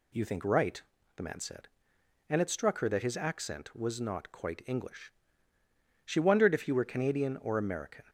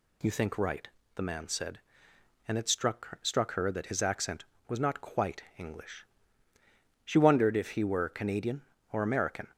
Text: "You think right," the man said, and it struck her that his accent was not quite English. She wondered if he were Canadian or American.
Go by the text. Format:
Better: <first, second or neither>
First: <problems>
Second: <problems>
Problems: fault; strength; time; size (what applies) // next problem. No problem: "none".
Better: first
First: none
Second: says "struck" twice; at 3.2 s // pauses between "quite" and "English"; slight; at 5.4 s; 0.16 s long